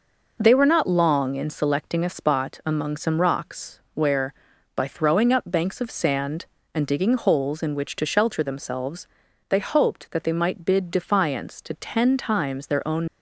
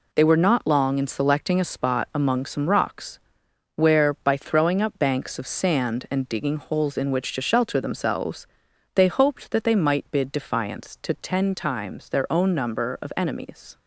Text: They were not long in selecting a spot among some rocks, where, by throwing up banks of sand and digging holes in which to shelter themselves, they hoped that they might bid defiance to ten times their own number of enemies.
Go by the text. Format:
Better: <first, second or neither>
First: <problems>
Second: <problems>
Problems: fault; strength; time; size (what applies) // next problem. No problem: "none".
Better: second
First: stops before "number of enemies"; at 13.0 s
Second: none